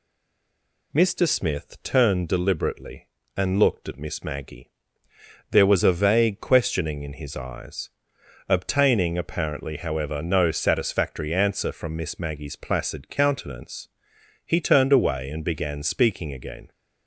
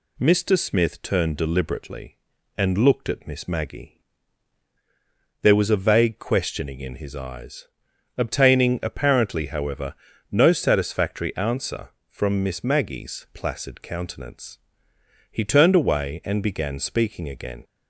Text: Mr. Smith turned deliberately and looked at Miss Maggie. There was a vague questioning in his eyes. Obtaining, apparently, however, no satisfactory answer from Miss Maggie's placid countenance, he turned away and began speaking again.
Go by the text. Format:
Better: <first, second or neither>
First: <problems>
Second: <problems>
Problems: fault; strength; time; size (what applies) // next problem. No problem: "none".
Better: second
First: stays silent before the first word; slight; until 0.9 s; 0.9 s long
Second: none